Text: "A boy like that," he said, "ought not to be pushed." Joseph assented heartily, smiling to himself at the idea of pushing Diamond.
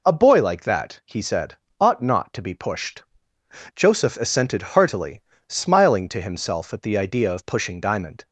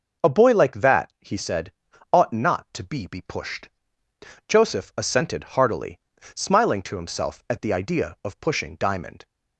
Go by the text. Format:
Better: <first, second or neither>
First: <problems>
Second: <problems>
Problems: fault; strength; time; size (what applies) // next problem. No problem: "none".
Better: first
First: none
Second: says "be" twice; at 3.0 s